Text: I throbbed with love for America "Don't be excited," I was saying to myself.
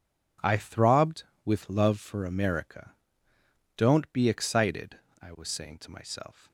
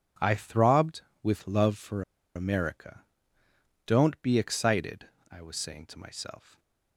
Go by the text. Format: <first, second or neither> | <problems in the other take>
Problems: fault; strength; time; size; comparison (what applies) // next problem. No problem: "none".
first | pauses between "for" and "America"; slight; at 2.0 s; 0.34 s long // pauses between "America" and "Don't"; noticeable; at 3.0 s; 0.82 s long; noticeable in the first